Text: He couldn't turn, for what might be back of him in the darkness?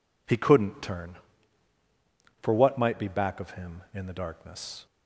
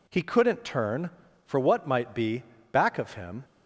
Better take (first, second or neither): first